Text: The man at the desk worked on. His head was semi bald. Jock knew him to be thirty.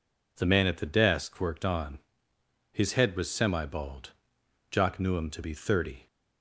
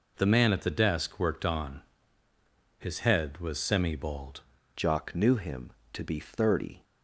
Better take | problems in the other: first | changes voice at "Jock"; from 4.7 s on; 2.1 s long

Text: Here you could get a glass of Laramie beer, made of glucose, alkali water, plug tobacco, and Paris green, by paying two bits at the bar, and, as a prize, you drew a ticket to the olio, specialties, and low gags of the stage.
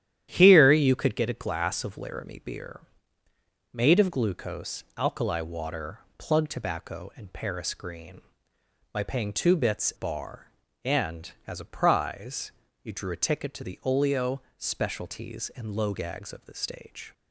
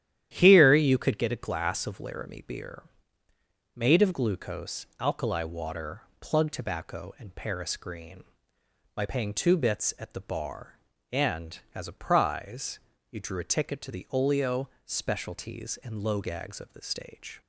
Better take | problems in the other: second | starts louder than the rest; strong; until 1.3 s; 11 dB; strong in the second // skips "at the"; at 9.9 s

